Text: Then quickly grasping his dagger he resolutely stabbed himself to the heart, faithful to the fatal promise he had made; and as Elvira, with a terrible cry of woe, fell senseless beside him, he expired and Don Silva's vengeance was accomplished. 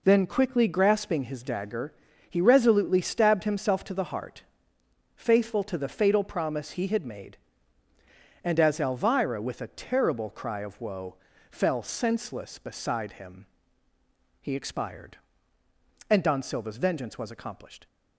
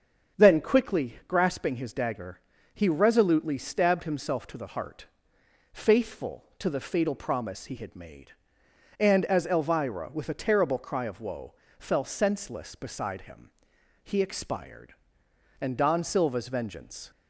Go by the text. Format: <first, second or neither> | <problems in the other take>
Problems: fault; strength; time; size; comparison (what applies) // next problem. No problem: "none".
first | starts louder than the rest; until 1.4 s; 6.5 dB // pauses between "dagger" and "he"; slight; at 2.4 s; 0.34 s long; slight in the first // stops before "was accomplished"; at 17.1 s